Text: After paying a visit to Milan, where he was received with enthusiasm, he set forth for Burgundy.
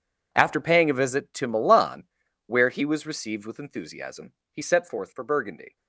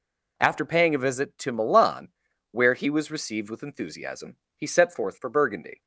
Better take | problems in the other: second | gets quieter; strong; throughout; 17.5 dB

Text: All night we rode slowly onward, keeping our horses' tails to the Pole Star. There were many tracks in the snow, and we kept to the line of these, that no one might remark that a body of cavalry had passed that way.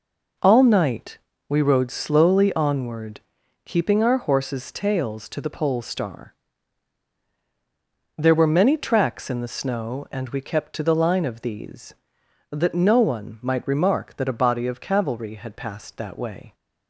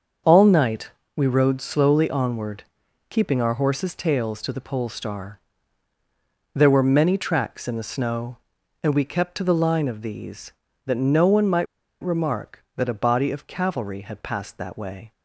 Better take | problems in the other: first | starts louder than the rest; until 1.5 s; 6.5 dB // pauses between "night" and "we"; slight; at 0.8 s; 0.26 s long; slight in the first // pauses between "might" and "remark"; at 11.6 s; 0.37 s long

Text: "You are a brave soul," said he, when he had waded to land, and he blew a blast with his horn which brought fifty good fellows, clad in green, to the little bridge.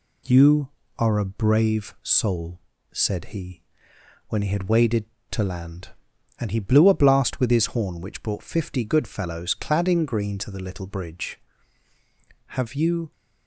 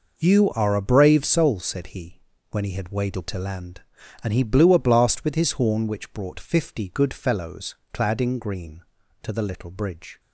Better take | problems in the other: second | goes on to say "Have you"; noticeable; from 12.4 s on; 0.64 s long

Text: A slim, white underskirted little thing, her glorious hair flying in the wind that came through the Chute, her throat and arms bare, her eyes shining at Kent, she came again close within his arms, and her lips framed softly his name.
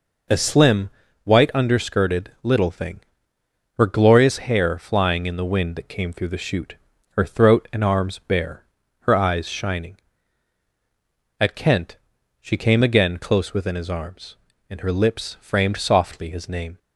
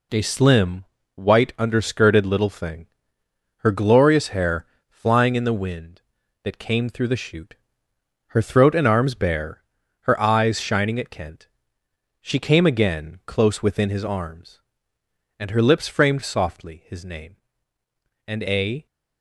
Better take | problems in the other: first | pauses between "hair" and "flying"; slight; at 4.6 s; 0.22 s long // goes on to say "And a"; from 18.2 s on; 0.58 s long

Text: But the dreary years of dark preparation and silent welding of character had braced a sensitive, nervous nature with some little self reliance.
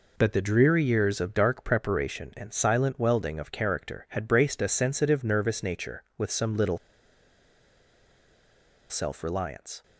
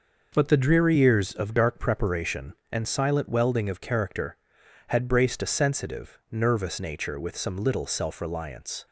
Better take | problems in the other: second | pauses between "little" and "self"; strong; at 6.7 s; 2.1 s long

